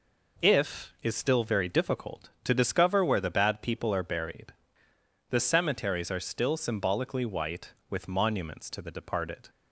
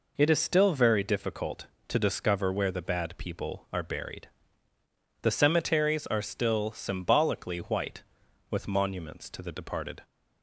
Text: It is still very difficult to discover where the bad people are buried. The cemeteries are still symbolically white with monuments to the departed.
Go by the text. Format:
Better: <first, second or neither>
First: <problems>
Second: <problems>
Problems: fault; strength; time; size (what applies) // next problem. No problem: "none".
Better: second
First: says "If" for "It"; at 0.4 s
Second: none